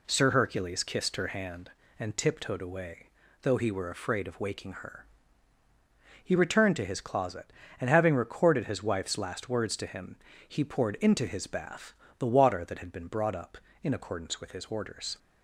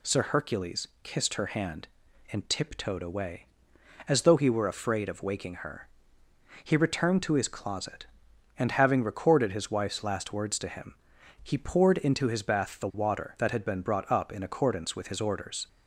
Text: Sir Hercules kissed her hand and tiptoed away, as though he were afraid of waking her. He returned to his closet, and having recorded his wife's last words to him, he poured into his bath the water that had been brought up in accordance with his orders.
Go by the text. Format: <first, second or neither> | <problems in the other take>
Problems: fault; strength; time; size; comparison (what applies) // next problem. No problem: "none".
second | skips "as"; at 3.2 s // pauses between "bath" and "the"; slight; at 11.9 s; 0.24 s long